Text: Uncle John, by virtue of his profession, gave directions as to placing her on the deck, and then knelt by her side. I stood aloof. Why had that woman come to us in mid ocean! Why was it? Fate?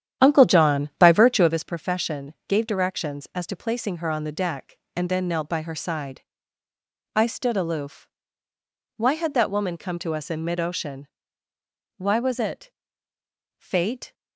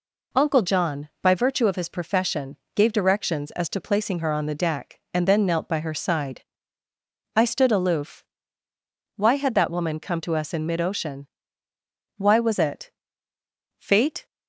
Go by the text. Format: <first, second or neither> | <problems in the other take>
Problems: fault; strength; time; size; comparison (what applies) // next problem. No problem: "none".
second | starts louder than the rest; strong; until 1.6 s; 10 dB